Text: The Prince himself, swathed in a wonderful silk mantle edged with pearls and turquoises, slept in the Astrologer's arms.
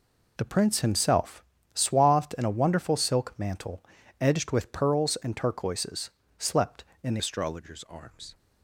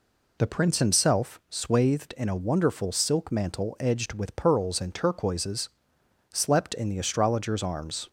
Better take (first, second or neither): second